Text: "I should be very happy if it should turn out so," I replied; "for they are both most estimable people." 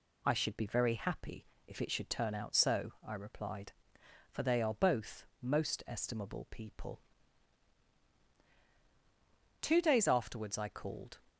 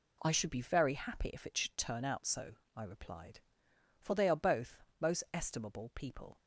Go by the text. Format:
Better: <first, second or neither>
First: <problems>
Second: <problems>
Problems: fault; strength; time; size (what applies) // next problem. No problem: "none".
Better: second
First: pauses between "happy" and "if"; slight; at 1.4 s; 0.20 s long // pauses between "both" and "most"; slight; at 5.2 s; 0.16 s long // goes on to say "Two days afterwards I called"; from 9.6 s on; 1.5 s long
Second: pauses between "both" and "most"; slight; at 4.7 s; 0.24 s long